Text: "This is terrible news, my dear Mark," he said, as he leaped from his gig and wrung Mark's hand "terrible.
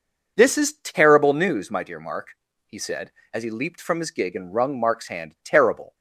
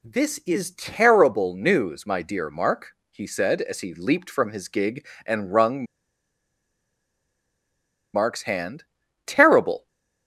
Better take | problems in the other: first | pauses between "wrung" and "Mark's"; strong; at 5.8 s; 2.2 s long // pauses between "hand" and "terrible"; at 8.8 s; 0.42 s long

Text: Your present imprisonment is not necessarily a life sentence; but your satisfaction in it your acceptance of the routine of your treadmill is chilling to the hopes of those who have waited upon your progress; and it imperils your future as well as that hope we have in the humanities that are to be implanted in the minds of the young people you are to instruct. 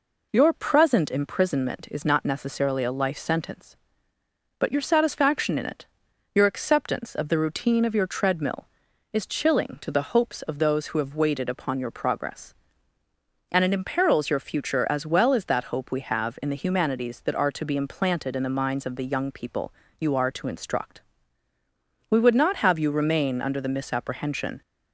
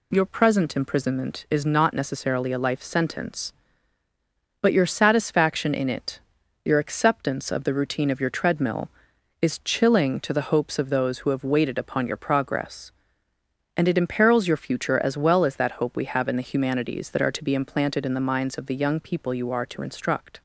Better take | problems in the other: second | pauses between "it" and "your"; noticeable; at 5.8 s; 0.48 s long; noticeable in the second // pauses between "people" and "you"; slight; at 19.7 s; 0.26 s long // goes on to say "We would not have you remain under the misapprehension"; strong; from 22.1 s on; 2.5 s long

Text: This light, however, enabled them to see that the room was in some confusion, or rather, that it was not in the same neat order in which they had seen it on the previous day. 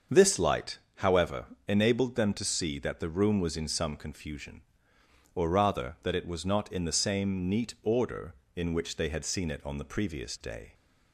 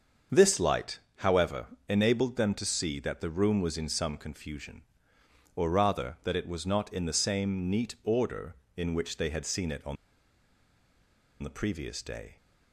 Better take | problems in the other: first | starts louder than the rest; until 1.5 s; 7 dB; also in the first // pauses between "on" and "the"; strong; at 9.9 s; 1.4 s long

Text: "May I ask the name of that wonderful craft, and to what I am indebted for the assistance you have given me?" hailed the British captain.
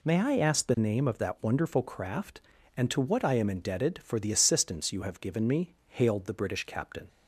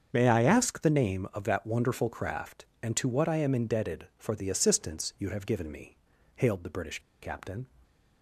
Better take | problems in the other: first | starts louder than the rest; strong; until 1.1 s; 7 dB // pauses between "British" and "captain"; slight; at 6.9 s; 0.22 s long

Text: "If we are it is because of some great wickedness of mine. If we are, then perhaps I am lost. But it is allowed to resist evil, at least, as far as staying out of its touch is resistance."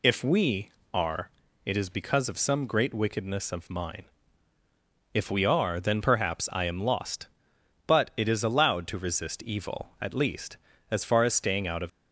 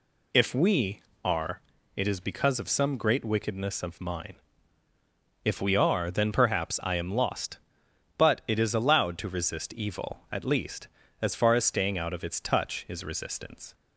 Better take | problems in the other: second | pauses between "are" and "it"; slight; at 1.3 s; 0.34 s long; slight in the second // stops before "its touch is resistance"; at 11.8 s

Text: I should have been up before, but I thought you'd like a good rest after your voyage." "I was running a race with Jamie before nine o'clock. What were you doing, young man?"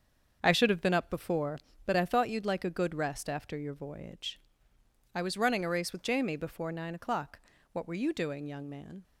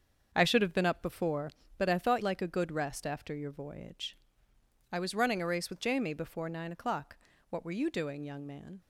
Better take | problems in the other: first | starts louder than the rest; until 1.3 s; 7 dB; also in the first // skips "you'd"; at 2.2 s

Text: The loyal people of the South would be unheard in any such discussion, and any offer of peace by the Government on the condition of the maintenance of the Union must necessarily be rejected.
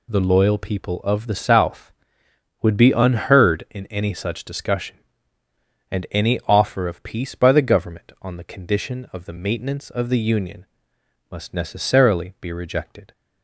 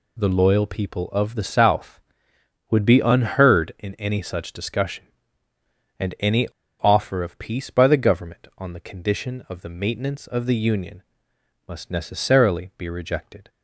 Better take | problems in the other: first | pauses between "any" and "offer"; slight; at 6.4 s; 0.35 s long // pauses between "Union" and "must"; noticeable; at 11.0 s; 0.66 s long; noticeable in the first

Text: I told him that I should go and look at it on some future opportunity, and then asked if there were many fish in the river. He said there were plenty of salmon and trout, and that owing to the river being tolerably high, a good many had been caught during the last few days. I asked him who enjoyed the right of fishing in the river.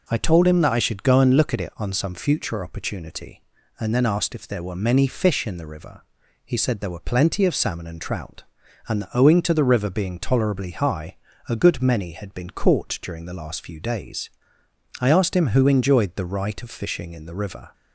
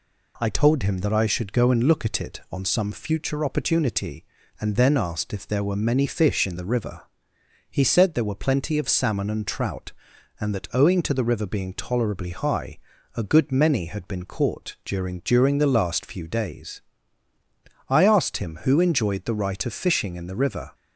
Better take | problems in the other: first | says "during" twice; at 15.1 s

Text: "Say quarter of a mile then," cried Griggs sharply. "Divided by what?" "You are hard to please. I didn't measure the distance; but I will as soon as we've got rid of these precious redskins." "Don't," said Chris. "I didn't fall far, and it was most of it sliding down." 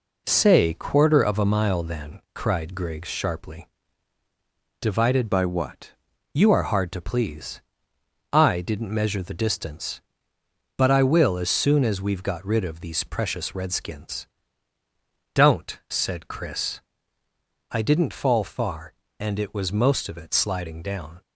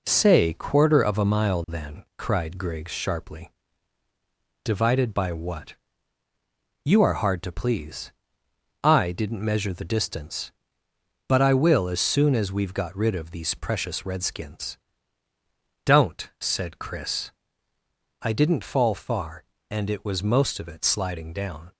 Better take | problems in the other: second | changes voice from "by" to "what"; from 5.3 to 5.9 s; 0.6 s long

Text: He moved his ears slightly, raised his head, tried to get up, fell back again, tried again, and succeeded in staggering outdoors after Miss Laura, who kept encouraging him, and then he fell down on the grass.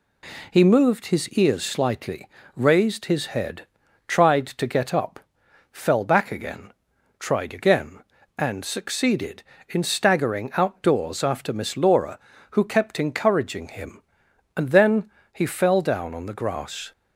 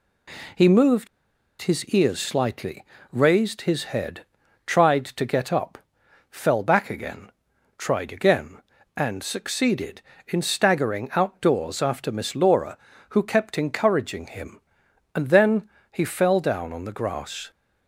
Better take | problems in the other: first | pauses between "moved" and "his"; noticeable; at 1.0 s; 0.54 s long // pauses between "then" and "he"; slight; at 15.6 s; 0.24 s long; slight in the first

